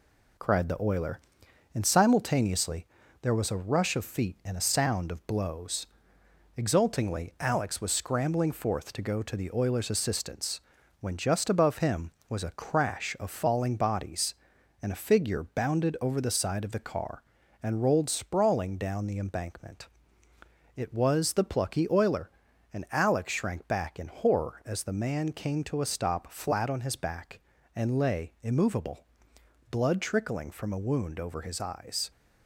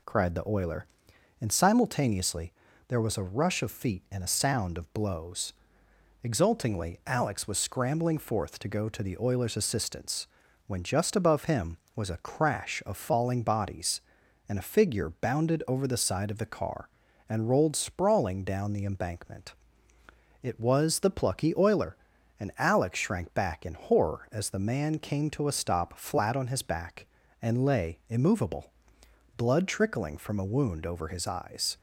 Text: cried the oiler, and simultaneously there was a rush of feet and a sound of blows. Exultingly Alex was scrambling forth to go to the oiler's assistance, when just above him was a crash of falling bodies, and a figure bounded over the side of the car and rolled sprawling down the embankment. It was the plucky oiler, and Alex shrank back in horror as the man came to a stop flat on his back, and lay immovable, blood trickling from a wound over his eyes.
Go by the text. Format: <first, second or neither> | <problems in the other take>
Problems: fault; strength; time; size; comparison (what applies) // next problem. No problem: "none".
second | gets quieter; noticeable; throughout; 4 dB // pauses between "simultaneously" and "there"; slight; at 2.8 s; 0.36 s long; slight in the second